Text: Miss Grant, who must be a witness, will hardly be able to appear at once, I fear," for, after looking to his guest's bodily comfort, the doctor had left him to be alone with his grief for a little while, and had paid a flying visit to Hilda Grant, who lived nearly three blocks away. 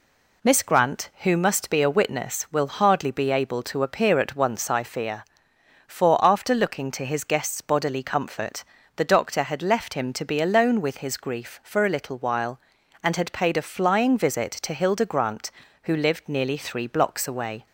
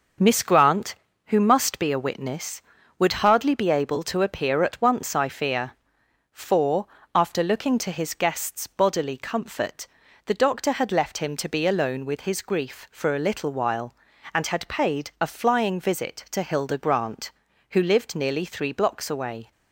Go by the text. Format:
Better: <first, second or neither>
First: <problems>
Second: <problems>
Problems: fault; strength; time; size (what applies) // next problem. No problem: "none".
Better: first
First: none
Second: starts louder than the rest; noticeable; until 1.5 s; 6 dB // says "would" for "will"; at 2.9 s